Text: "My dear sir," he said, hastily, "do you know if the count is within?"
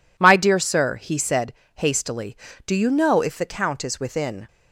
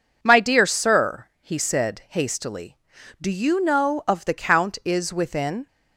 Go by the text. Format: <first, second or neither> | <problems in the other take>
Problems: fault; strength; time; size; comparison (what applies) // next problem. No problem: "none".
first | says "of" for "if"; at 4.0 s